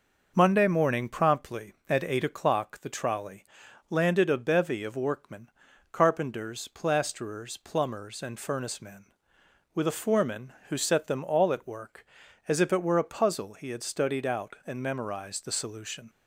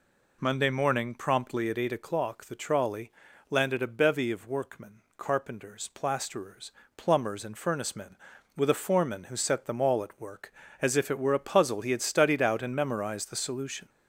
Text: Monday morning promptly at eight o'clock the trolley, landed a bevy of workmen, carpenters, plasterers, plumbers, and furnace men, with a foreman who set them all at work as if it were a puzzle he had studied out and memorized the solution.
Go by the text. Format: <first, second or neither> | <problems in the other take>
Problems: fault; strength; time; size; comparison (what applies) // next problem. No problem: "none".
first | gets louder; slight; throughout; 2.5 dB